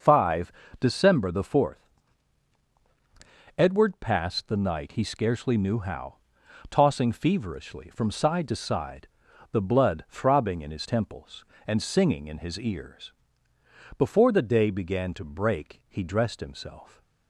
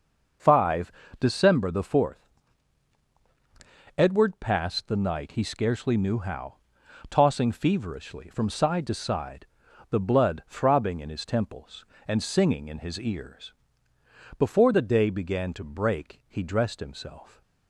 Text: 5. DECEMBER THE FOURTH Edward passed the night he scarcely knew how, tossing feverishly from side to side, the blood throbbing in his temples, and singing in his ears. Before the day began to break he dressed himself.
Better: neither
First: pauses between "FOURTH" and "Edward"; strong; at 1.8 s; 1.6 s long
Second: pauses between "FOURTH" and "Edward"; strong; at 2.2 s; 1.6 s long

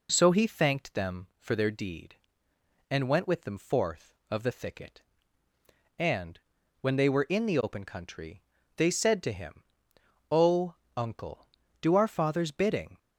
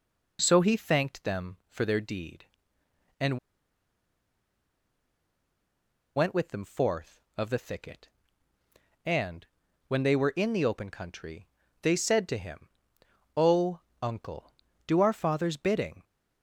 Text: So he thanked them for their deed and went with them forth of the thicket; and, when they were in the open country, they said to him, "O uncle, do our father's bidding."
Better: first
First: pauses between "O" and "uncle"; slight; at 10.7 s; 0.24 s long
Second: pauses between "and" and "went"; strong; at 3.3 s; 2.7 s long // pauses between "O" and "uncle"; slight; at 13.7 s; 0.24 s long

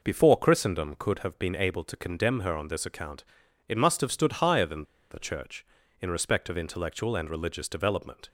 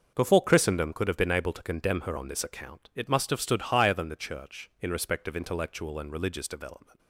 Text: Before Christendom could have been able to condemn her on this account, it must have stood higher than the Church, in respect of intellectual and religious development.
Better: second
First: pauses between "than" and "the"; slight; at 4.8 s; 0.27 s long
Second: none

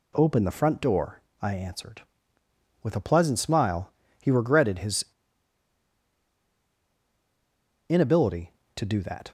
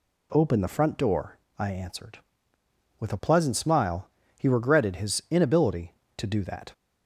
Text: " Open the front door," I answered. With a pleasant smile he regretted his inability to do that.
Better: second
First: pauses between "smile" and "he"; slight; at 3.9 s; 0.32 s long // pauses between "his" and "inability"; strong; at 5.0 s; 2.8 s long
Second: pauses between "smile" and "he"; slight; at 4.0 s; 0.32 s long

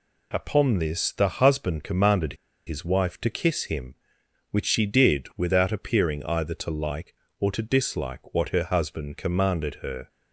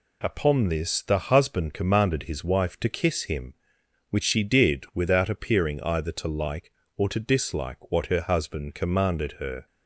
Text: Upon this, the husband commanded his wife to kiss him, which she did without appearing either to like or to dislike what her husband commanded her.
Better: second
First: pauses between "commanded" and "his"; slight; at 2.3 s; 0.32 s long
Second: none

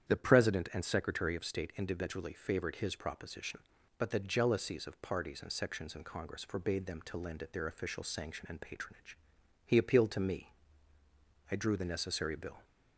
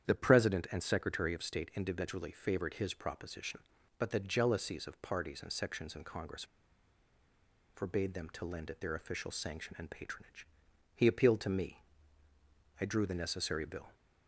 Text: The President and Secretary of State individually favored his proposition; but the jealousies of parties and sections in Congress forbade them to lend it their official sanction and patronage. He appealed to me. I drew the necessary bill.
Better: first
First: starts louder than the rest; strong; until 1.1 s; 9 dB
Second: starts louder than the rest; strong; until 1.0 s; 9 dB // pauses between "Congress" and "forbade"; strong; at 6.4 s; 1.3 s long

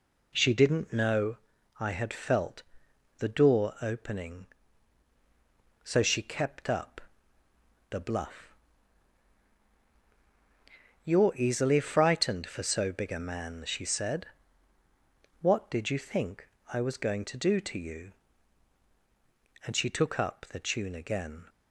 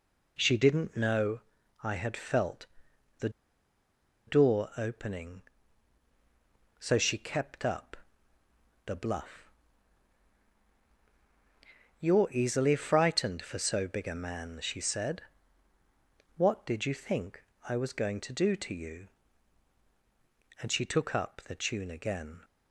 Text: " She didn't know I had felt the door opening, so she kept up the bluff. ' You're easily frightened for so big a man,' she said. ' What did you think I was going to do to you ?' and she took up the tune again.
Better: first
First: pauses between "know" and "I"; at 1.3 s; 0.40 s long // pauses between "felt" and "the"; noticeable; at 2.6 s; 0.52 s long // pauses between "up" and "the"; noticeable; at 7.0 s; 0.88 s long // pauses between "think" and "I"; slight; at 16.4 s; 0.24 s long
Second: pauses between "know" and "I"; at 1.4 s; 0.40 s long // pauses between "felt" and "the"; noticeable; at 2.6 s; 0.50 s long // pauses between "the" and "door"; noticeable; at 3.2 s; 0.97 s long // pauses between "up" and "the"; noticeable; at 7.9 s; 0.88 s long // pauses between "think" and "I"; slight; at 17.4 s; 0.24 s long

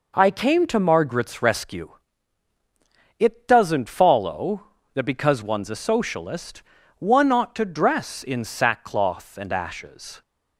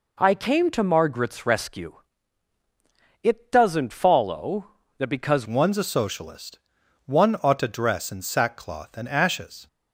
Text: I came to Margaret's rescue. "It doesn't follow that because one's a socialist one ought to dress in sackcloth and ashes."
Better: first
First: pauses between "socialist" and "one"; at 6.6 s; 0.38 s long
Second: changes voice at "one's"; from 5.4 s on; 4.2 s long // pauses between "socialist" and "one"; noticeable; at 6.5 s; 0.48 s long

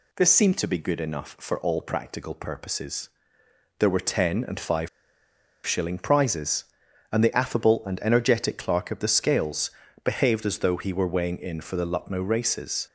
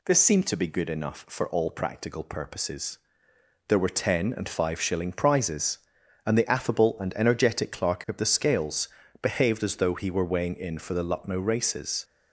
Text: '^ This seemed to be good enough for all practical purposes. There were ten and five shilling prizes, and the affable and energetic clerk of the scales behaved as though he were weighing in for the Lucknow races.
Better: second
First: pauses between "five" and "shilling"; noticeable; at 4.8 s; 0.77 s long // pauses between "scales" and "behaved"; slight; at 9.7 s; 0.32 s long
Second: pauses between "scales" and "behaved"; slight; at 8.8 s; 0.32 s long

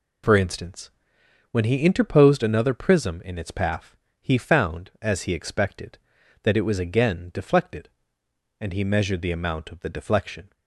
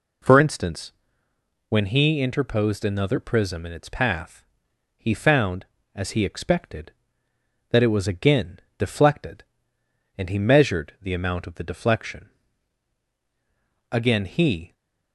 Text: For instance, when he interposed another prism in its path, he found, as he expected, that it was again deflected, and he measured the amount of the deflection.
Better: first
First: none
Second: pauses between "again" and "deflected"; slight; at 8.5 s; 0.18 s long // goes on to say "Again he"; noticeable; from 13.9 s on; 0.82 s long

